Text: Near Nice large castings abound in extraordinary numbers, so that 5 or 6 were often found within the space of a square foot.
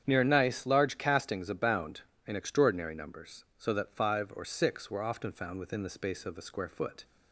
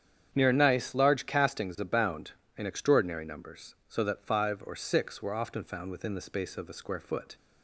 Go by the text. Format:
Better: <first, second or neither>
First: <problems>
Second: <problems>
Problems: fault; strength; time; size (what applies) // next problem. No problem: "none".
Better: neither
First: starts louder than the rest; strong; until 1.0 s; 8.5 dB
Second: starts louder than the rest; strong; until 1.3 s; 8.5 dB